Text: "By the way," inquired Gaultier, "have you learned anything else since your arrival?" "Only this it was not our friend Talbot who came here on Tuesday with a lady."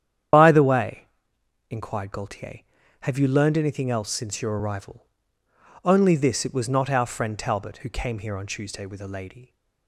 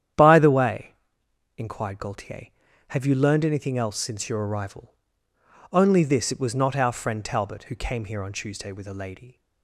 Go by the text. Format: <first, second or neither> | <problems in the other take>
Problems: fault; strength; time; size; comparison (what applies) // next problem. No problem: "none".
second | loses the start of "By"; at 0.3 s; 55 ms // starts louder than the rest; strong; until 1.9 s; 9.5 dB; strong in the second